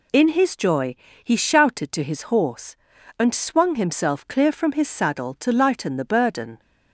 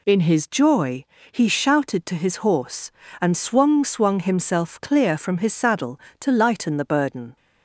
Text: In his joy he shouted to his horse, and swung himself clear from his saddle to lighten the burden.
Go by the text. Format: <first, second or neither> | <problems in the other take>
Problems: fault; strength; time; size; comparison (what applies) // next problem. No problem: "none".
first | pauses between "joy" and "he"; slight; at 1.0 s; 0.26 s long; slight in the first // says "swung" twice; at 3.8 s